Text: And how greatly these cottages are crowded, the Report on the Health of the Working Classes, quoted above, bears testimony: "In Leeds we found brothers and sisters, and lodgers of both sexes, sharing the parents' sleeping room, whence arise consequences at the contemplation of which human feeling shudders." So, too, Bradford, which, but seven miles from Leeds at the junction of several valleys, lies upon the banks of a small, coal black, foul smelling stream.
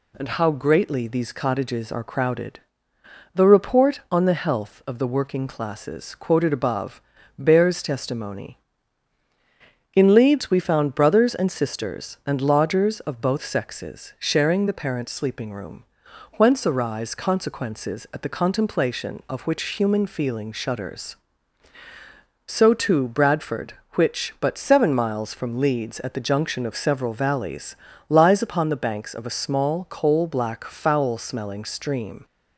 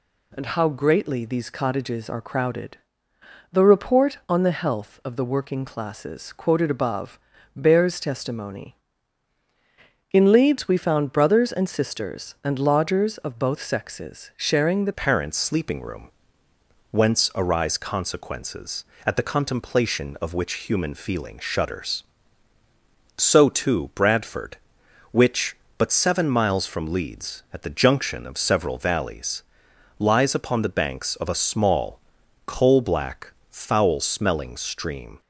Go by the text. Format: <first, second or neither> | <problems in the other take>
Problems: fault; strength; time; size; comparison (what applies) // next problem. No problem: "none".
first | changes voice at "parents"; from 14.9 s on; 20.3 s long